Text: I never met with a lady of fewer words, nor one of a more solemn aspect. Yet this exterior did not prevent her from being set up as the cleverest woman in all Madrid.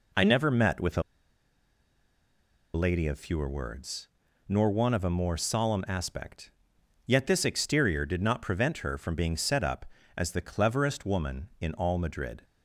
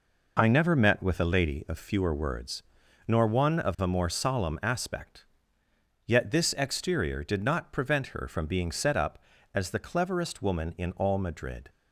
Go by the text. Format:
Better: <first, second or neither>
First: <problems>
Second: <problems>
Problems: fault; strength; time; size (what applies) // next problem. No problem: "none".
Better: second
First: pauses between "a" and "lady"; strong; at 1.0 s; 1.7 s long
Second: none